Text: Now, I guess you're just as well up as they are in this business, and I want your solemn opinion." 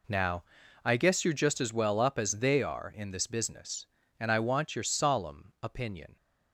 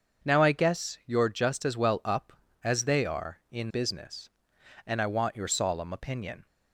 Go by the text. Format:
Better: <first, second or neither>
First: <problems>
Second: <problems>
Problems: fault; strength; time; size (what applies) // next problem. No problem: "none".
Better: first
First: none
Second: starts louder than the rest; until 1.3 s; 6.5 dB // skips "this"; at 3.7 s